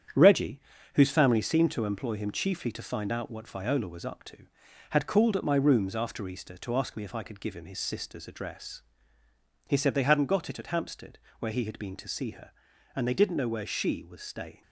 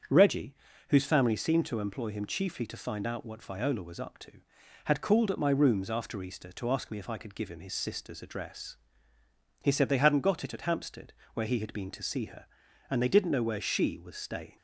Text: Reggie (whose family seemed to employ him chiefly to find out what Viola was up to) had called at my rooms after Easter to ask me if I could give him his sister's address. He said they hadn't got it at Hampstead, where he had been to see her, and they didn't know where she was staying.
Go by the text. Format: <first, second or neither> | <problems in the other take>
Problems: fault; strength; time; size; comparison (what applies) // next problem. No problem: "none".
second | gets quieter; throughout; 6.5 dB // starts louder than the rest; strong; until 1.5 s; 8.5 dB; strong in the second